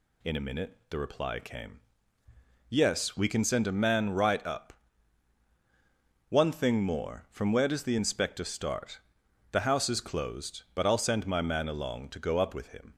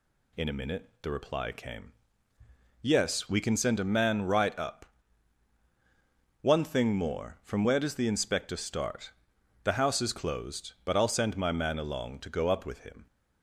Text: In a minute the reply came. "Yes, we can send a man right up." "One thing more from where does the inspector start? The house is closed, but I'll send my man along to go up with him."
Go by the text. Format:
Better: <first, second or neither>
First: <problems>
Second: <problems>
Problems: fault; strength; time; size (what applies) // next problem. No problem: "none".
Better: neither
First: none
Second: none